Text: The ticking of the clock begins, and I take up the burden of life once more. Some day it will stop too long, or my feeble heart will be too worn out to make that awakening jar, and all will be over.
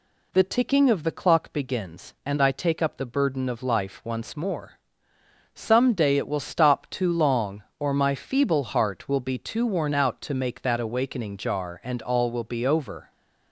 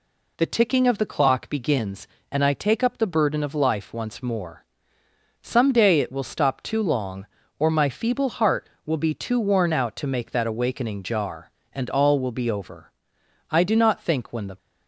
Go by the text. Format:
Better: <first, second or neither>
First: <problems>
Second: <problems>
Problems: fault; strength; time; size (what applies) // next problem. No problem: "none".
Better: first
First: none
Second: goes on to say "I do not think when the"; noticeable; from 13.4 s on; 1.0 s long